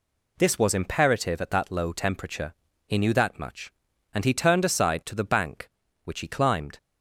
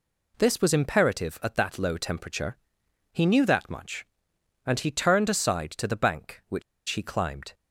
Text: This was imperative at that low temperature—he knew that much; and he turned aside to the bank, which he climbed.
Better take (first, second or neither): first